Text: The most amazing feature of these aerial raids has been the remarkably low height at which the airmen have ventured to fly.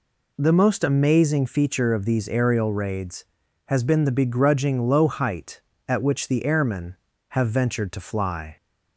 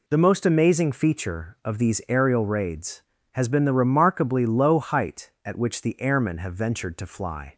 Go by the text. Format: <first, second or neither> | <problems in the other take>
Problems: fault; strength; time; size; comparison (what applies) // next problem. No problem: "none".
second | says "begrudging" for "remarkably"; at 4.1 s